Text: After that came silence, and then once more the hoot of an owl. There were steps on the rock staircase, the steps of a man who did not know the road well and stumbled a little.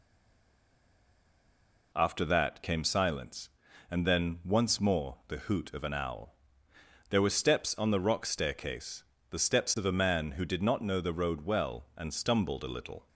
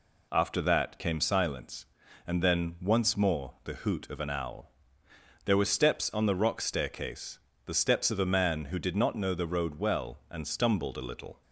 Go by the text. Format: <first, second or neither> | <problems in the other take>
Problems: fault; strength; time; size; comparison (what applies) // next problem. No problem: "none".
second | stays silent before the first word; noticeable; until 1.9 s; 1.9 s long